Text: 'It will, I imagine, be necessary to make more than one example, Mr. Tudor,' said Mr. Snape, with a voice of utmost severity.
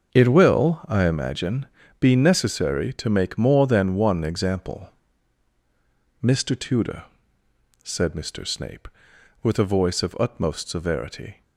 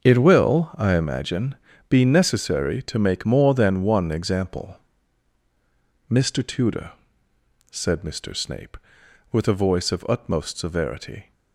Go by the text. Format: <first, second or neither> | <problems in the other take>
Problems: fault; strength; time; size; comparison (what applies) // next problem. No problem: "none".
neither | starts louder than the rest; the same in both